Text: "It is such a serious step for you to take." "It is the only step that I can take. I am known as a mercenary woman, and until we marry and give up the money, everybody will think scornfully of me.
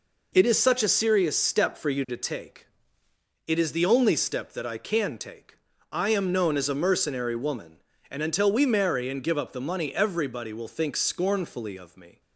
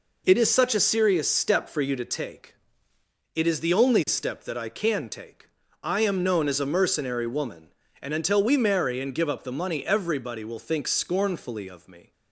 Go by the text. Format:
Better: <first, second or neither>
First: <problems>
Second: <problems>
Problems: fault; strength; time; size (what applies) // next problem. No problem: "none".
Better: neither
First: none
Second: none